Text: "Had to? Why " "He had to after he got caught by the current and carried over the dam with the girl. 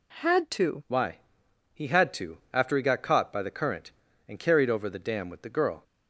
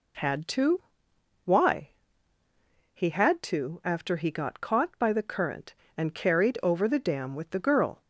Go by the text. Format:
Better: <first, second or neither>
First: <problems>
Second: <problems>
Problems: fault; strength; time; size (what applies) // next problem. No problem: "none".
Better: second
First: changes voice at "Why"; from 0.8 s on; 5.0 s long // pauses between "to" and "after"; slight; at 2.3 s; 0.16 s long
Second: none